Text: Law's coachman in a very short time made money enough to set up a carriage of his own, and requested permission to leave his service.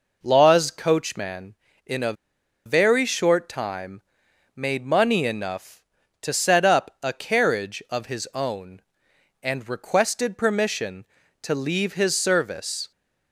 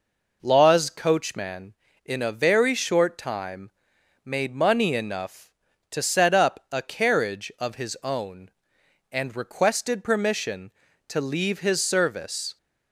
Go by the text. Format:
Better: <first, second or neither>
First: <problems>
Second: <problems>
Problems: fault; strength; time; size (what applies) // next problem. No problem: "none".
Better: second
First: pauses between "a" and "very"; noticeable; at 2.1 s; 0.52 s long // pauses between "time" and "made"; noticeable; at 4.0 s; 0.54 s long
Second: pauses between "time" and "made"; noticeable; at 3.6 s; 0.54 s long